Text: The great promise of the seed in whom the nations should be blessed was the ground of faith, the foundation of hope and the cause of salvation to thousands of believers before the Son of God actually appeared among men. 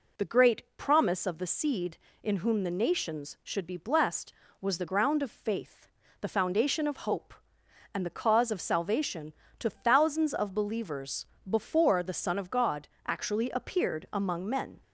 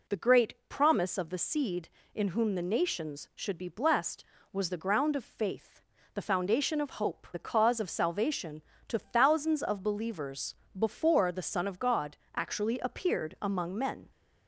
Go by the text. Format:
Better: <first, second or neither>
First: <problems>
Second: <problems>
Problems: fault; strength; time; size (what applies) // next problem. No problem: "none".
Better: first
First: pauses between "great" and "promise"; slight; at 0.6 s; 0.16 s long // pauses between "believers" and "before"; slight; at 11.2 s; 0.24 s long // pauses between "God" and "actually"; slight; at 12.8 s; 0.18 s long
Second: pauses between "great" and "promise"; slight; at 0.5 s; 0.16 s long // skips "and"; at 7.3 s // pauses between "believers" and "before"; slight; at 10.5 s; 0.24 s long // pauses between "God" and "actually"; slight; at 12.1 s; 0.18 s long